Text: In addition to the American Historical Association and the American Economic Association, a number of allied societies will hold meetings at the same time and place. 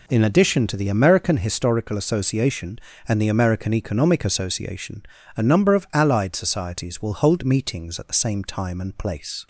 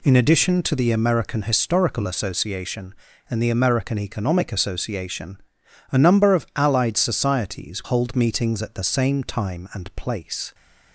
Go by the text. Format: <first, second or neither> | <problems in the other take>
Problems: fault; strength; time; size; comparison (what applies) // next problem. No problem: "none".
first | skips "will"; at 7.8 s